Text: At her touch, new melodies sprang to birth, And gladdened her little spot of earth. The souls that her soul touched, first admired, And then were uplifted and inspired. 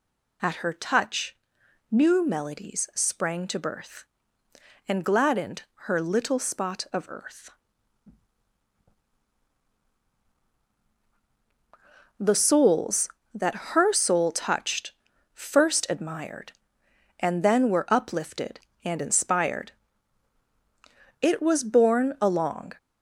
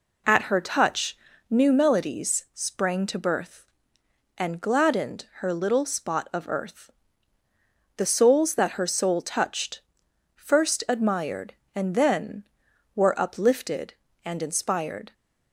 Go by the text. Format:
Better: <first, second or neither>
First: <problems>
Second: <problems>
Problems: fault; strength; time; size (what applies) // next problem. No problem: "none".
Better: second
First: pauses between "gladdened" and "her"; slight; at 5.6 s; 0.22 s long // goes on to say "It was borne along"; from 21.1 s on; 1.5 s long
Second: none